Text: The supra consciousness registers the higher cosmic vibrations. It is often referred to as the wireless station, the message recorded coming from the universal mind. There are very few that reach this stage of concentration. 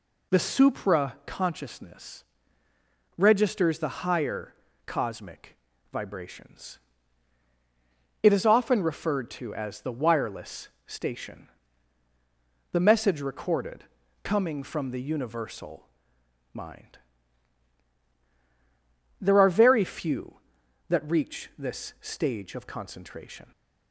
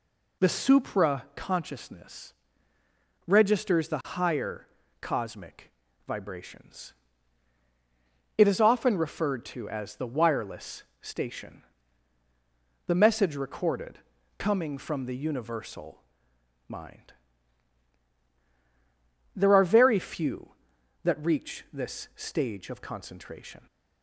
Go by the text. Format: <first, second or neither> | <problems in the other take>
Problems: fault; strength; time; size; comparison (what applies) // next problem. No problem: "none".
neither | pauses between "consciousness" and "registers"; noticeable; the same in both // pauses between "higher" and "cosmic"; slight; the same in both // pauses between "cosmic" and "vibrations"; the same in both // pauses between "wireless" and "station"; slight; the same in both // pauses between "recorded" and "coming"; the same in both // pauses between "universal" and "mind"; noticeable; the same in both